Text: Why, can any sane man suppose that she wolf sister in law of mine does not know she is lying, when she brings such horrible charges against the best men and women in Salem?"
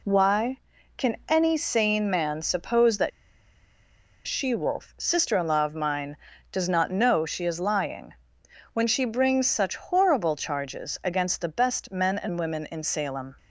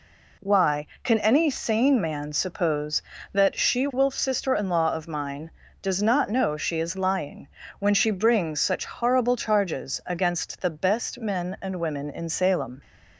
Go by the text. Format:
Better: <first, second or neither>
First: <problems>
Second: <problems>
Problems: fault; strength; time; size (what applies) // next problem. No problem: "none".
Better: second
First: pauses between "that" and "she"; at 3.1 s; 1.1 s long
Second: none